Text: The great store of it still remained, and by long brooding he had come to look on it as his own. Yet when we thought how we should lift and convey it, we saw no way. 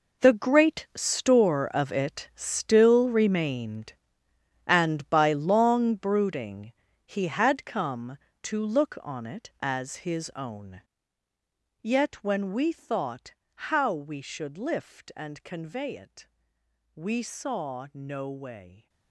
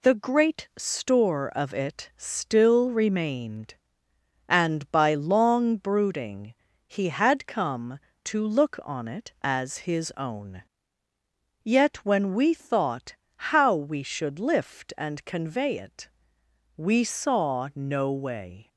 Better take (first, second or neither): second